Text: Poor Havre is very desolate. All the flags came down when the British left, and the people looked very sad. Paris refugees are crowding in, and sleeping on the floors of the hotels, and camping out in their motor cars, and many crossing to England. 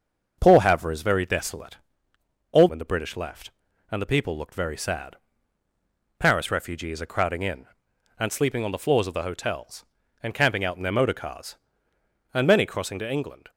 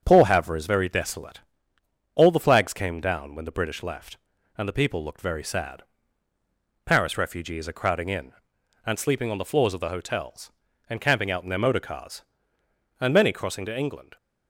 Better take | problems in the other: second | starts louder than the rest; until 1.4 s; 6.5 dB; also in the second // skips "the flags came down"; at 2.6 s

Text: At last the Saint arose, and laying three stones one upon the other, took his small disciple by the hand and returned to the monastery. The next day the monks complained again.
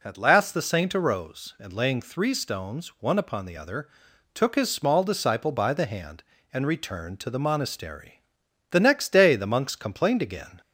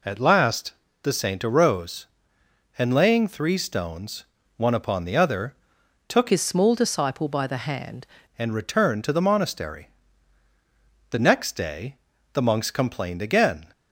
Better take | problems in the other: first | pauses between "last" and "the"; slight; at 0.7 s; 0.30 s long // pauses between "stones" and "one"; slight; at 4.2 s; 0.32 s long // changes voice from "his" to "hand"; from 6.2 to 8.0 s; 1.8 s long // pauses between "day" and "the"; slight; at 11.9 s; 0.36 s long

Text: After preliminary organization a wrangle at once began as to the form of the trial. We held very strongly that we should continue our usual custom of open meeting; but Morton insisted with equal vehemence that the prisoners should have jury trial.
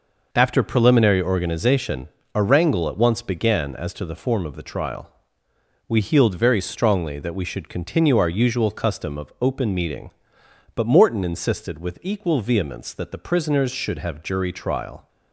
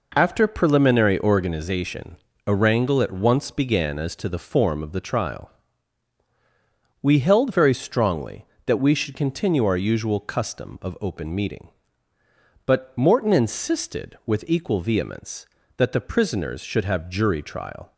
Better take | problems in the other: second | pauses between "organization" and "a"; slight; at 2.0 s; 0.26 s long; slight in the second // says "healed" for "held"; at 5.9 s

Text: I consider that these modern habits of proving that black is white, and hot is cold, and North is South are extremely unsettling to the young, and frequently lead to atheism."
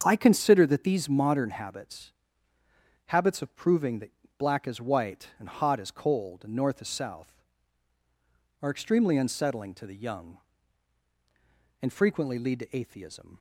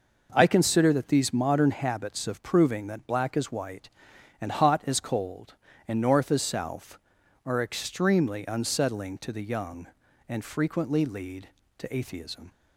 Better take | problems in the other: second | starts louder than the rest; strong; until 1.0 s; 7.5 dB // says "habits" twice; at 3.0 s // pauses between "that" and "black"; slight; at 4.0 s; 0.28 s long

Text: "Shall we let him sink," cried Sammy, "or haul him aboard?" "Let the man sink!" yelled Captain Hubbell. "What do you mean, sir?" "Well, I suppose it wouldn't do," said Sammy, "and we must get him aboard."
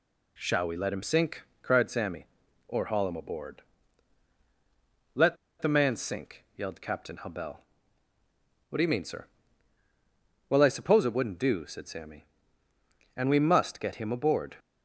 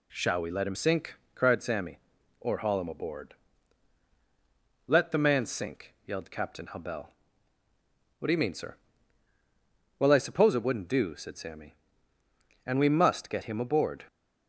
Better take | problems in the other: second | pauses between "Let" and "the"; slight; at 5.3 s; 0.25 s long

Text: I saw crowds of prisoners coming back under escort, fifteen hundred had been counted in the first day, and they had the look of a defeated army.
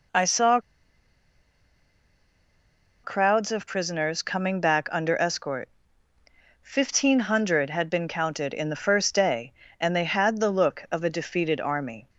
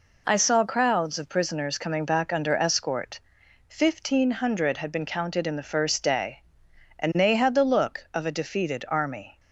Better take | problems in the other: second | pauses between "saw" and "crowds"; strong; at 0.5 s; 2.4 s long

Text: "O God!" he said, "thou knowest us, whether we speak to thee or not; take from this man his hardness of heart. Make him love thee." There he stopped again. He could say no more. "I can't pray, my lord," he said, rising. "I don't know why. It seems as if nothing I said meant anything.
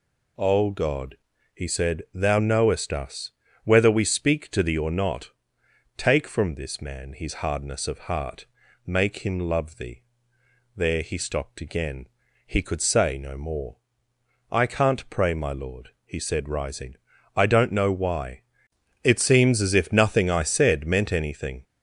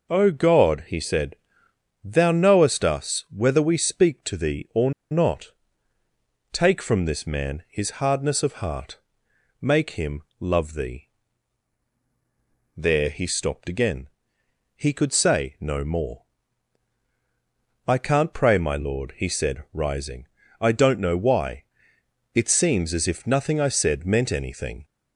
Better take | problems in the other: first | pauses between "or" and "not"; slight; at 4.9 s; 0.20 s long // pauses between "him" and "love"; slight; at 10.2 s; 0.16 s long

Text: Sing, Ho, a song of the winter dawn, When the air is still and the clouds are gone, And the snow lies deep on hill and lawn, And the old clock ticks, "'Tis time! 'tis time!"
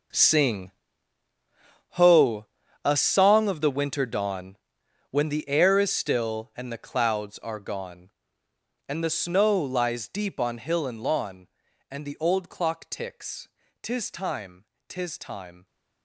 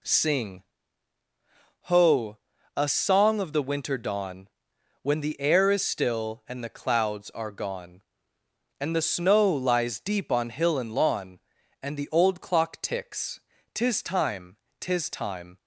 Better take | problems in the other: second | gets quieter; strong; throughout; 13.5 dB

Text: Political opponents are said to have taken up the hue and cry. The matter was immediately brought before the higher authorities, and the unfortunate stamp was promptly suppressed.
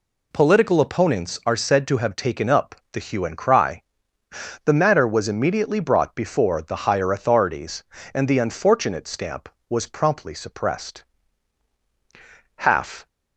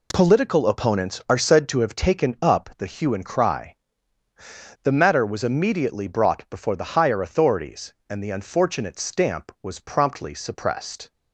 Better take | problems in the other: second | pauses between "up" and "the"; slight; at 2.7 s; 0.18 s long // goes on to say "Half"; from 12.5 s on; 0.50 s long

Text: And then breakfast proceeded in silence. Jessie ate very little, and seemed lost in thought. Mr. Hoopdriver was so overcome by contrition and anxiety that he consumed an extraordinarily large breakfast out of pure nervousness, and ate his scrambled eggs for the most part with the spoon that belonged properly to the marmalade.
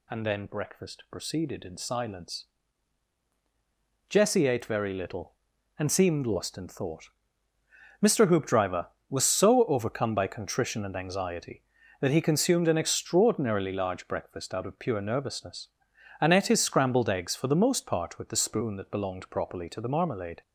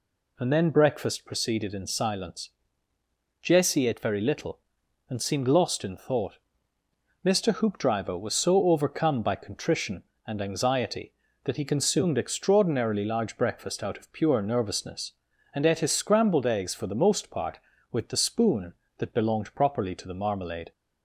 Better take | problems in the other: first | skips "an"; at 12.1 s

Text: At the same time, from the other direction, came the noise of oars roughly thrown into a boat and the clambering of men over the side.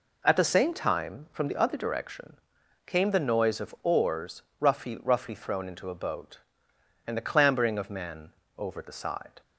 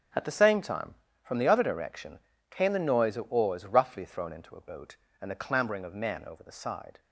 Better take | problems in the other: second | pauses between "oars" and "roughly"; slight; at 4.4 s; 0.20 s long // says "roughly" twice; at 5.0 s // pauses between "men" and "over"; slight; at 8.2 s; 0.28 s long

